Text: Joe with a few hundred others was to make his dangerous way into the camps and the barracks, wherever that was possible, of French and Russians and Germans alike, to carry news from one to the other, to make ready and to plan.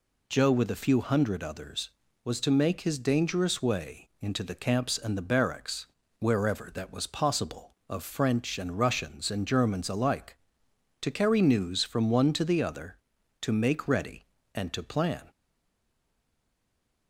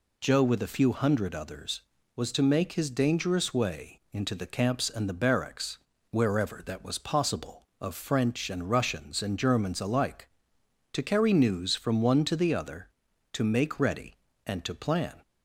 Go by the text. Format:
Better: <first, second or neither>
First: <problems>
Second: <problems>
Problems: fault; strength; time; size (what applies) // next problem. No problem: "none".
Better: second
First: stays silent after the last word; noticeable; from 15.3 s on; 1.7 s long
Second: none